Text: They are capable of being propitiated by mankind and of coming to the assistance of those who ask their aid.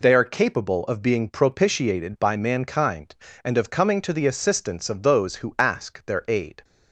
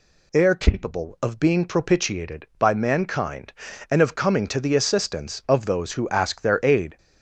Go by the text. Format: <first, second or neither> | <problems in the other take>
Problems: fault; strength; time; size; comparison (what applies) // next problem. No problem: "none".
neither | none